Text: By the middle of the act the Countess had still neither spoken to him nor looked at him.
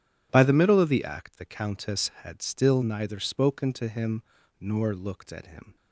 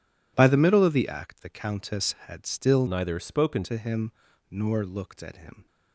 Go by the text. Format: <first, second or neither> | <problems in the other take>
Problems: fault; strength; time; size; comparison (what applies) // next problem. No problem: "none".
first | changes voice from "neither" to "spoken"; from 2.8 to 3.6 s; 0.8 s long // pauses between "him" and "nor"; at 4.0 s; 0.40 s long; also in the first